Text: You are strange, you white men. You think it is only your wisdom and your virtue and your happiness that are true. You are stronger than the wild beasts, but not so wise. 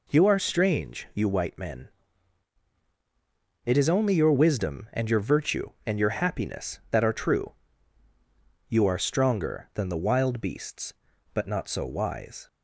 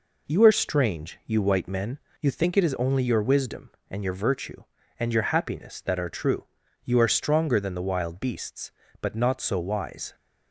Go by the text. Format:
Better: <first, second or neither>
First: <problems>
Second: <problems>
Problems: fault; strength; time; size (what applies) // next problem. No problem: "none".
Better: second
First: skips "You think"; at 2.7 s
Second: none